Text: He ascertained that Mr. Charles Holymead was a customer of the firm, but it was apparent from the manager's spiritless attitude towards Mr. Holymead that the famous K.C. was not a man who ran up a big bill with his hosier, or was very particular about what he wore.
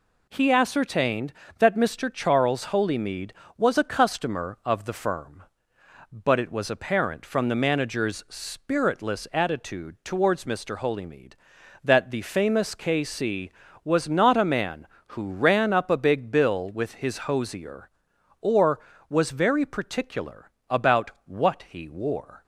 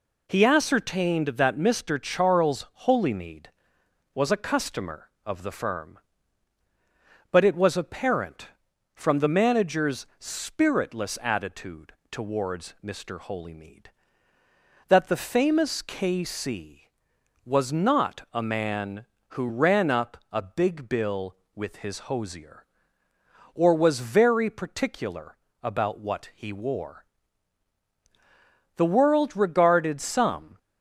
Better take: first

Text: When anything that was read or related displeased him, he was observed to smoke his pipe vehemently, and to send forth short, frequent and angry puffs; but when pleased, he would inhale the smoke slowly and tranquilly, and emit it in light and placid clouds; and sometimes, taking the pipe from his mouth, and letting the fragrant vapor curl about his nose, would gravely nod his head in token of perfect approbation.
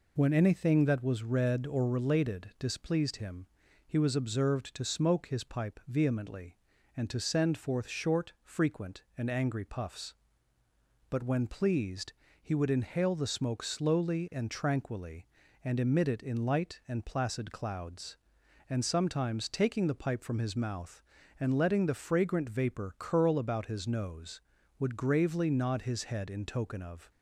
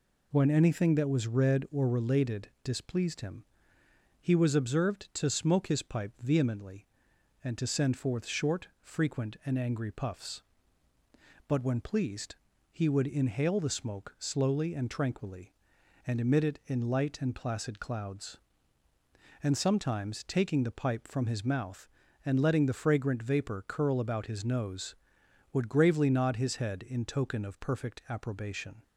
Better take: second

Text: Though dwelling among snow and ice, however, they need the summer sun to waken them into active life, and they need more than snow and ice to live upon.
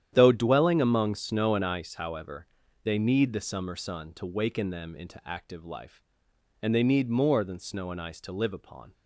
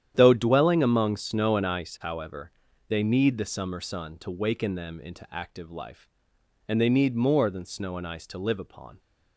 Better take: neither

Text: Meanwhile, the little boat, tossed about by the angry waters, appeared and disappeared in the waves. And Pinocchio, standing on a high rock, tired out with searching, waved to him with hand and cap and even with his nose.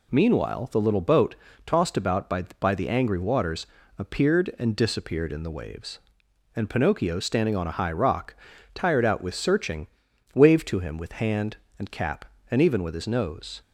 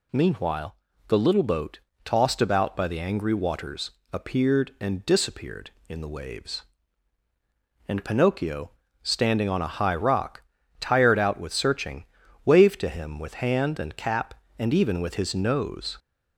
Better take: second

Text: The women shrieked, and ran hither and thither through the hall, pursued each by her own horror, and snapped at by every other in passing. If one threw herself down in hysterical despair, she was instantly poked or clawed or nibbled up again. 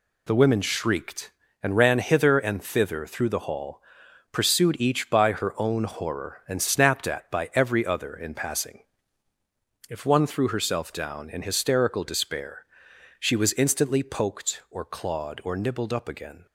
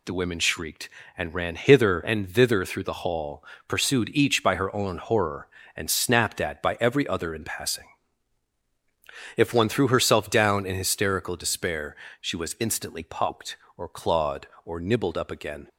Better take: neither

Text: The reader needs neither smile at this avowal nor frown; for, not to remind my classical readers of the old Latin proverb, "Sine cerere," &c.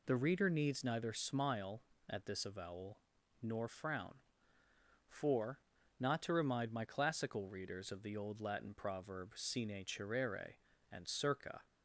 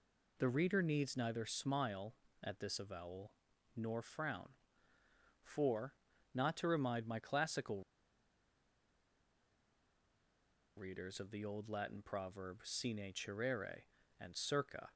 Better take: first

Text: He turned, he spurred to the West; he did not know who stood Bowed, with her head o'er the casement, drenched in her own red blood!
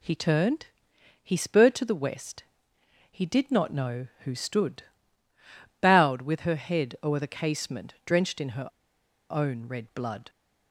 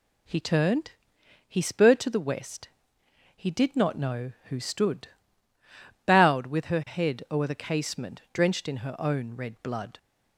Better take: second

